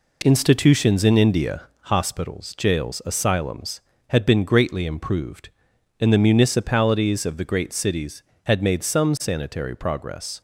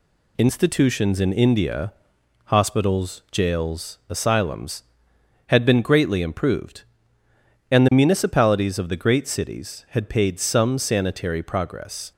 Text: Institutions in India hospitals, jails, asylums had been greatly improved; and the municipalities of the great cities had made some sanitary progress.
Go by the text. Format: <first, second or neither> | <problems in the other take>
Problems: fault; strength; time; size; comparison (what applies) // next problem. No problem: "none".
first | pauses between "India" and "hospitals"; noticeable; at 1.9 s; 0.56 s long; slight in the first // says "paid" for "made"; at 10.0 s